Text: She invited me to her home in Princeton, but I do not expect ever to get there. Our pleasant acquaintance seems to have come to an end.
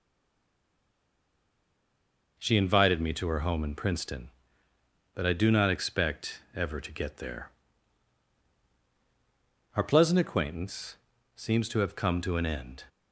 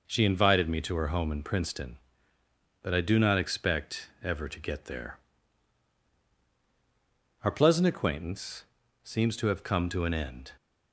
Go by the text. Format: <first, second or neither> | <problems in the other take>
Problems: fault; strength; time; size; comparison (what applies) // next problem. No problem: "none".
second | stays silent before the first word; until 2.3 s; 2.3 s long // pauses between "acquaintance" and "seems"; at 10.9 s; 0.38 s long; also in the second